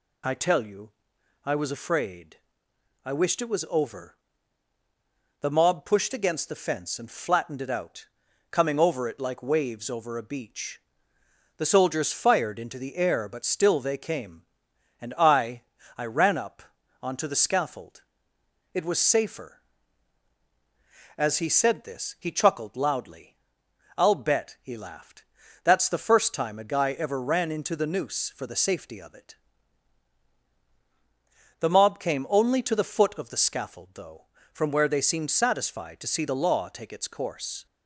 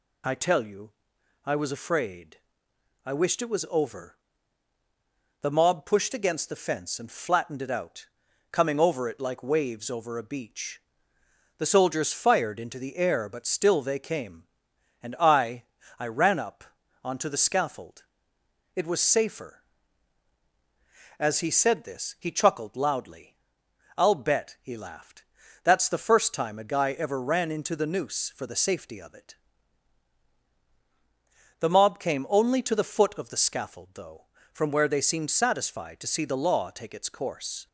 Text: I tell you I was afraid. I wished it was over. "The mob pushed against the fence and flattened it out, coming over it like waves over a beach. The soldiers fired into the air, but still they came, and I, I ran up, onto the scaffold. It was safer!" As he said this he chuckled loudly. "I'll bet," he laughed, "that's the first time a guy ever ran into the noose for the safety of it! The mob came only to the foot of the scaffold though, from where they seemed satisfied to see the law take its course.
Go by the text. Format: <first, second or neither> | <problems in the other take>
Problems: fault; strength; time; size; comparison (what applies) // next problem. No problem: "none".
neither | pauses between "you" and "I"; noticeable; the same in both